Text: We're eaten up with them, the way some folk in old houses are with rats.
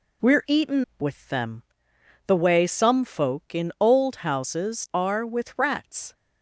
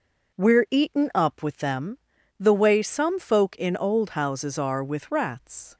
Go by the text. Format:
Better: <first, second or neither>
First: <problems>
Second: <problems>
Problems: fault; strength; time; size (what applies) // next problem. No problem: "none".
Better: second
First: skips "up"; at 0.9 s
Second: none